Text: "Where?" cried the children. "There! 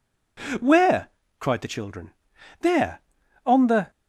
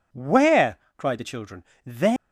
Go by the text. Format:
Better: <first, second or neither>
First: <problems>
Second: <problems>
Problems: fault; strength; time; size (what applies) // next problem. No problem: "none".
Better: second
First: goes on to say "On the"; slight; from 3.4 s on; 0.46 s long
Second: none